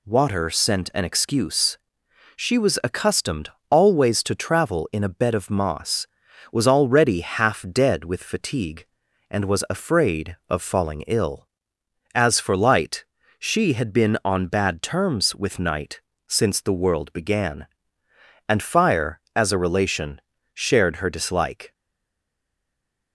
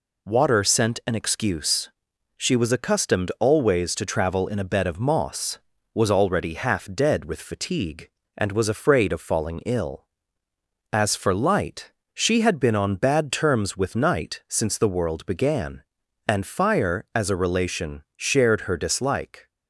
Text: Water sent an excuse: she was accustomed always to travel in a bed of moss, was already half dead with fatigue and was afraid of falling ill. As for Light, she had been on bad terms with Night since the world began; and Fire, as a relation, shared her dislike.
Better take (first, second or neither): second